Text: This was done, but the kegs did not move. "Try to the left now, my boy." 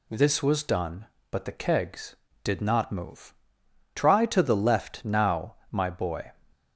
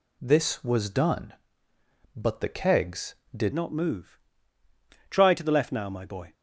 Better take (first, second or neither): first